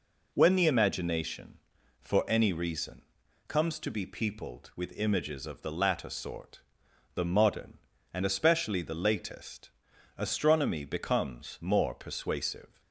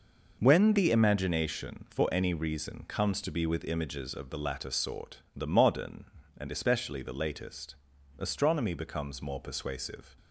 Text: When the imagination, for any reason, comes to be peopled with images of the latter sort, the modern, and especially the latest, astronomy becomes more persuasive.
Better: first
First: none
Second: skips "peopled"; at 3.4 s

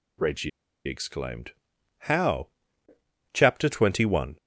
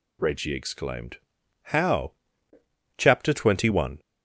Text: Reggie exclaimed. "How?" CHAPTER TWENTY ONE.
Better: second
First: pauses between "Reggie" and "exclaimed"; at 0.4 s; 0.36 s long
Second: none

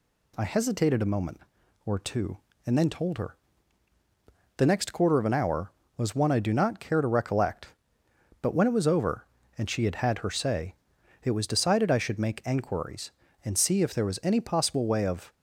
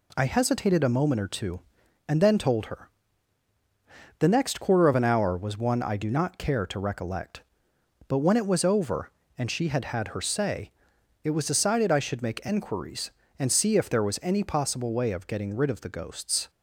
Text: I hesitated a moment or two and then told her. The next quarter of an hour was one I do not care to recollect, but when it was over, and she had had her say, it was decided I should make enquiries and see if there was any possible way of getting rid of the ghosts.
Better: second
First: stops before "getting rid of the ghosts"; at 15.3 s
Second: none

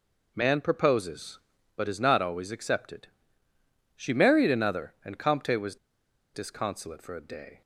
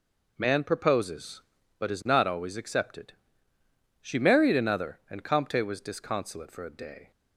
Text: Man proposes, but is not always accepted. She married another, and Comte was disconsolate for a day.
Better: second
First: pauses between "was" and "disconsolate"; noticeable; at 5.7 s; 0.59 s long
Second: none

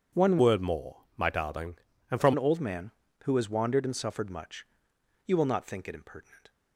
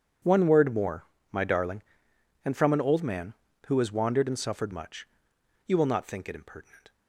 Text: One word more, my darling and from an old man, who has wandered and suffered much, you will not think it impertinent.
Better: second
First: changes voice from "word" to "from"; from 0.3 to 2.3 s; 2.0 s long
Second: none

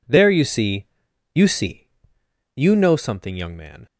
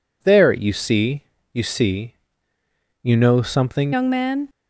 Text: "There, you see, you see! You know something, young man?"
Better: first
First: none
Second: changes voice at "young"; from 3.9 s on; 0.5 s long

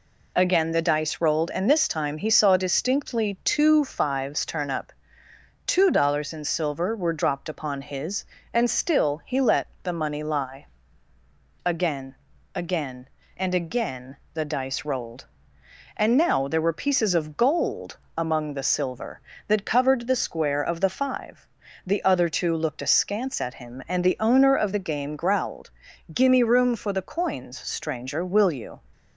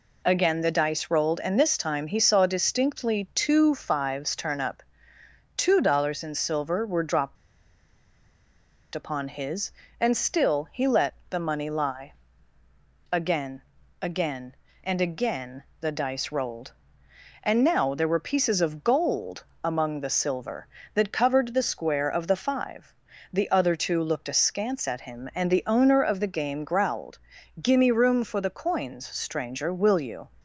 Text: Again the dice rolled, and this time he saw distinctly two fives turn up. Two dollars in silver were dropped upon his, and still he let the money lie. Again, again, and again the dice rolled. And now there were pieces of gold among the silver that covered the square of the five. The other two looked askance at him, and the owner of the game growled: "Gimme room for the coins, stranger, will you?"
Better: first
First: pauses between "let" and "the"; slight; at 9.6 s; 0.18 s long // pauses between "again" and "the"; slight; at 14.1 s; 0.18 s long // pauses between "gold" and "among"; slight; at 17.9 s; 0.18 s long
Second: pauses between "dropped" and "upon"; strong; at 7.3 s; 1.5 s long // pauses between "let" and "the"; slight; at 11.1 s; 0.18 s long // pauses between "again" and "the"; slight; at 15.6 s; 0.18 s long // pauses between "gold" and "among"; slight; at 19.4 s; 0.18 s long

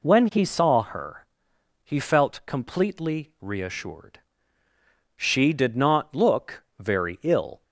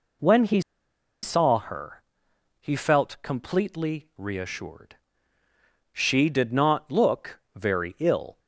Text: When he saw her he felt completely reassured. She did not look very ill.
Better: first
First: pauses between "her" and "he"; noticeable; at 1.2 s; 0.58 s long // pauses between "look" and "very"; slight; at 6.6 s; 0.16 s long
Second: pauses between "he" and "saw"; noticeable; at 0.6 s; 0.62 s long // pauses between "her" and "he"; noticeable; at 2.0 s; 0.58 s long // pauses between "look" and "very"; slight; at 7.3 s; 0.16 s long

